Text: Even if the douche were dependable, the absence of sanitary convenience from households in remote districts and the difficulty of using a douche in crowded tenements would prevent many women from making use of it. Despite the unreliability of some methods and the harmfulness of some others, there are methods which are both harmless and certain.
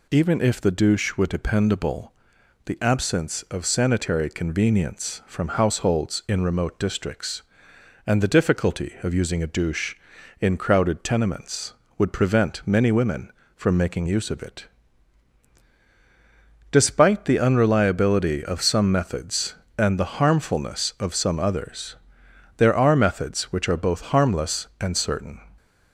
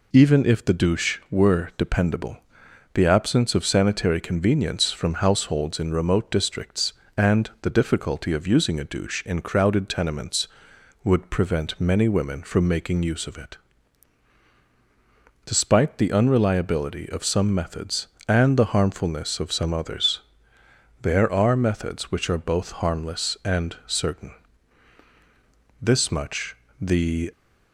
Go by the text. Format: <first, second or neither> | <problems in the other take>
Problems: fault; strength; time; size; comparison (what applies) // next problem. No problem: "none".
first | goes on to say "This much the"; from 25.7 s on; 1.5 s long